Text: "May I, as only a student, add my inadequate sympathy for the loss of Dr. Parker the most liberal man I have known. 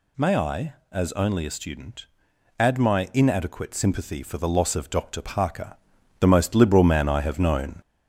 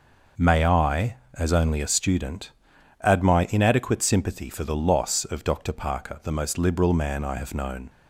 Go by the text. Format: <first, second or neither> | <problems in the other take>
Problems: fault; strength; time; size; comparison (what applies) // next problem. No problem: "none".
second | gets louder; slight; throughout; 2.5 dB // pauses between "Parker" and "the"; noticeable; at 5.7 s; 0.46 s long